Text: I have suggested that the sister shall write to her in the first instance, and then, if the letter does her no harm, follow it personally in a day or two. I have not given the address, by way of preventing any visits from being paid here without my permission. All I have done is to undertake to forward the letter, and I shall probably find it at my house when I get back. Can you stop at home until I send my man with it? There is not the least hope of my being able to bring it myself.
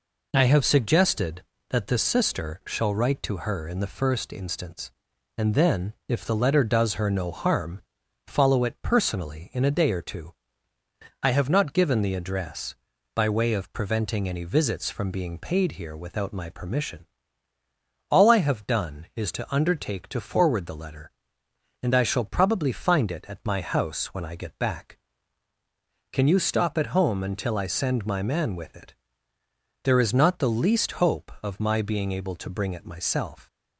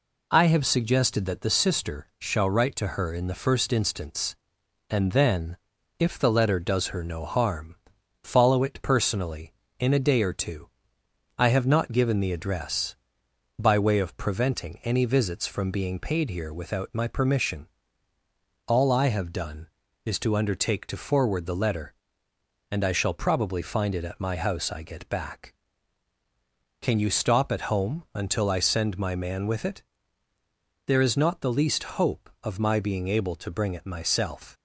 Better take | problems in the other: first | skips "when"; at 24.7 s

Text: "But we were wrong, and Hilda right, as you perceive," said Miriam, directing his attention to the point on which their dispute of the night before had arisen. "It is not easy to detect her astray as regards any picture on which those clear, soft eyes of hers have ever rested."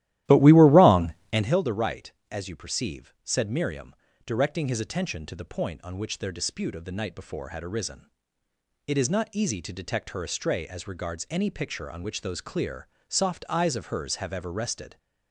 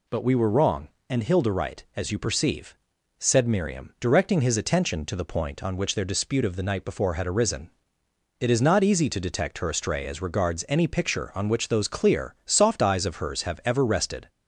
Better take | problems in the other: second | starts louder than the rest; strong; until 1.6 s; 14 dB

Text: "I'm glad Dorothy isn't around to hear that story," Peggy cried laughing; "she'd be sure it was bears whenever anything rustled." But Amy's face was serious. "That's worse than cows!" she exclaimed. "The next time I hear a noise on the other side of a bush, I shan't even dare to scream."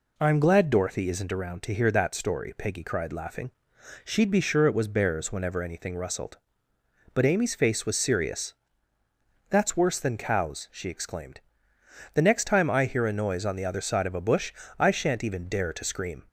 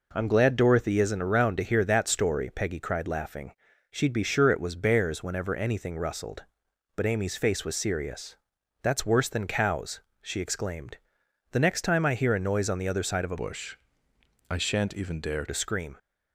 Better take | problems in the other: first | changes voice from "bush" to "dare"; from 13.3 to 15.4 s; 2.1 s long

